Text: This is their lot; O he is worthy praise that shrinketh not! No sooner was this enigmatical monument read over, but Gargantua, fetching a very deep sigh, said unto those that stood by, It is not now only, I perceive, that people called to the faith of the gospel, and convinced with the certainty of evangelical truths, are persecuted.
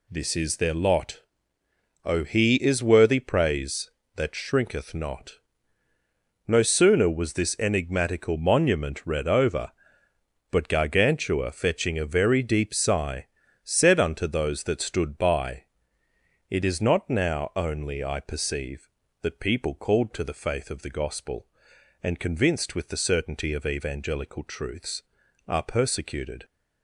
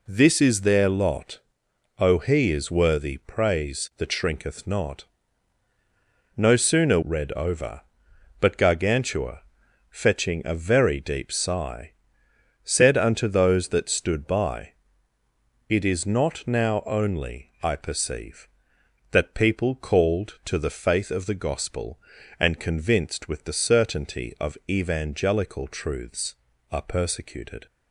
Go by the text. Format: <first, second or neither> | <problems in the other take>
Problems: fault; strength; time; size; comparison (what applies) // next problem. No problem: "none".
first | skips "was this enigmatical monument"; at 7.0 s